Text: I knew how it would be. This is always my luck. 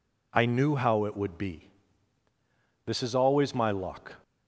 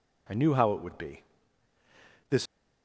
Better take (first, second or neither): first